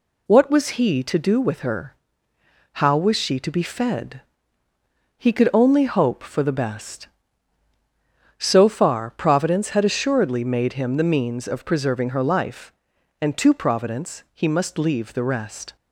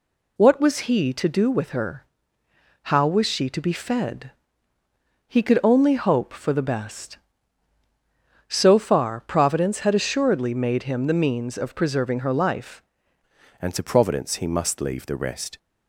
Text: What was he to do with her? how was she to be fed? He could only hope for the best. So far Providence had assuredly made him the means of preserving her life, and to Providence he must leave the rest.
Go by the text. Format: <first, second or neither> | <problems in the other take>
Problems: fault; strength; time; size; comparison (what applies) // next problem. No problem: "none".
first | changes voice at "and"; from 13.6 s on; 1.9 s long